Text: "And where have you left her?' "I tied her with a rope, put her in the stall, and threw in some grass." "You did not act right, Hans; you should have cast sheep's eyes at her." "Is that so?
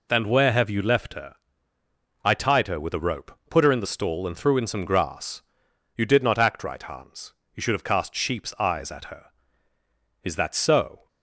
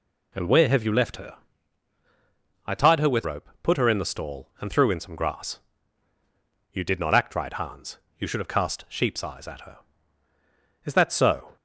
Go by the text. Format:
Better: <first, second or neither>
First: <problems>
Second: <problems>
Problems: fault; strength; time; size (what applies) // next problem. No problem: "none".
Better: first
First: none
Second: skips "a"; at 3.2 s